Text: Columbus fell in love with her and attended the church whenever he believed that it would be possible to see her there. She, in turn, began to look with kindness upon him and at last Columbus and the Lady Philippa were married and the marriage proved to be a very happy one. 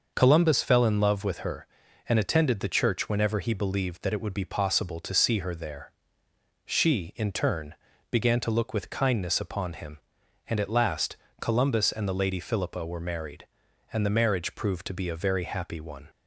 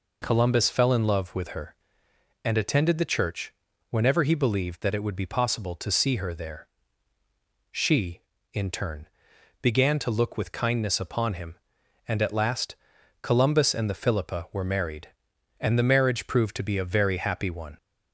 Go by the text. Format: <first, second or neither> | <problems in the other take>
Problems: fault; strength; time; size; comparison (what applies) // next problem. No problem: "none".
first | pauses between "church" and "whenever"; at 3.5 s; 0.38 s long // pauses between "last" and "Columbus"; at 12.7 s; 0.44 s long; slight in the first // skips "Lady"; at 13.9 s